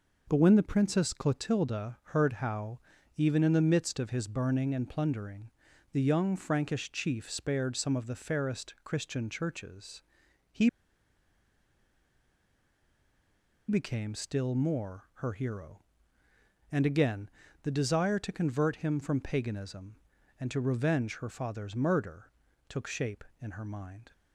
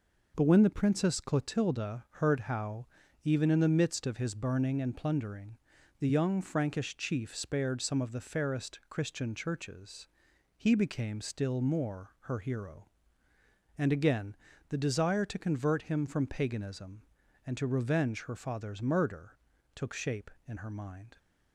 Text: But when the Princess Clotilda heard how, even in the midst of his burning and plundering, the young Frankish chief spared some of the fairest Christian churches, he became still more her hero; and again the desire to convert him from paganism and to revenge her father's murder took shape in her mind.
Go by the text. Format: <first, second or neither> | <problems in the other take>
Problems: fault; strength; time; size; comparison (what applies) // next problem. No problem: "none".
second | pauses between "Clotilda" and "heard"; slight; at 1.9 s; 0.16 s long; slight in the second // pauses between "he" and "became"; strong; at 10.6 s; 2.9 s long // pauses between "again" and "the"; slight; at 17.2 s; 0.34 s long; slight in the second // pauses between "murder" and "took"; at 22.3 s; 0.38 s long; also in the second